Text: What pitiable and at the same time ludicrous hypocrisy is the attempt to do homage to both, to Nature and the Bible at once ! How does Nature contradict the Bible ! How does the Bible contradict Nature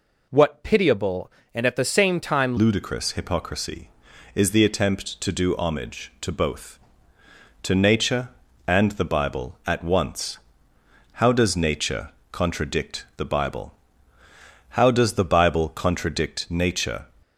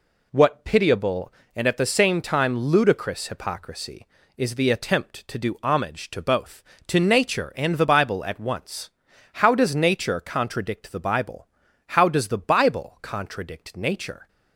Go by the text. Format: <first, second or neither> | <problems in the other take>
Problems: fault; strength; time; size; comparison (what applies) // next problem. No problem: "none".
second | changes voice at "ludicrous"; from 2.5 s on; 14.5 s long // pauses between "Nature" and "contradict"; slight; at 12.0 s; 0.22 s long